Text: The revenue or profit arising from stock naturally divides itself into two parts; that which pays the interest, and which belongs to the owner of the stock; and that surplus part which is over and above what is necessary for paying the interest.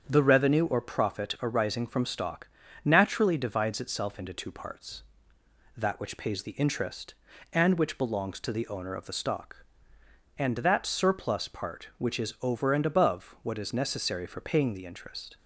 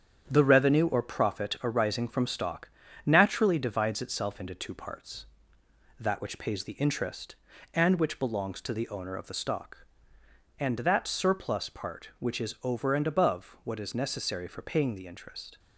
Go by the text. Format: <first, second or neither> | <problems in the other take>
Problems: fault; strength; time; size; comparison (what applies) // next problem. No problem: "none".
first | gets quieter; noticeable; throughout; 5.5 dB // starts louder than the rest; strong; until 1.2 s; 8.5 dB; strong in the first // pauses between "stock" and "naturally"; slight; at 2.6 s; 0.36 s long; slight in the first